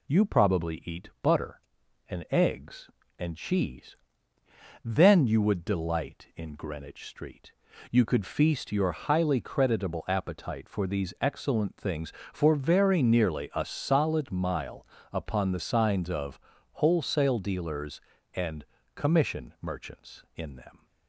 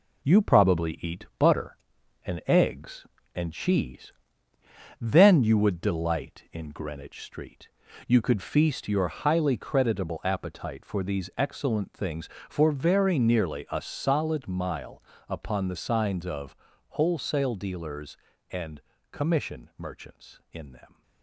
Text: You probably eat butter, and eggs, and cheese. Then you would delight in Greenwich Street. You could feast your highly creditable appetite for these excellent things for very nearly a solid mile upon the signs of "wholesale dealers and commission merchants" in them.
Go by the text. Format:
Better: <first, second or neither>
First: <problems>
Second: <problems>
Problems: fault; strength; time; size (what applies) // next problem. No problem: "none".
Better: first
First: pauses between "mile" and "upon"; slight; at 14.8 s; 0.26 s long // pauses between "of" and "wholesale"; slight; at 16.3 s; 0.34 s long // pauses between "and" and "commission"; slight; at 18.6 s; 0.30 s long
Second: gets quieter; throughout; 6 dB // pauses between "mile" and "upon"; slight; at 15.0 s; 0.26 s long // pauses between "of" and "wholesale"; slight; at 16.5 s; 0.34 s long // pauses between "and" and "commission"; slight; at 18.7 s; 0.30 s long